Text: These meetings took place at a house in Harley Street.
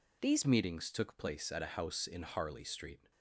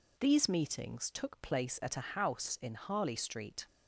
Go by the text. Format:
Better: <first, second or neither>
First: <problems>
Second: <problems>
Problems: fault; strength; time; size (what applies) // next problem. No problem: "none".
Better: second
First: changes voice at "meetings"; from 0.4 s on; 2.7 s long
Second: none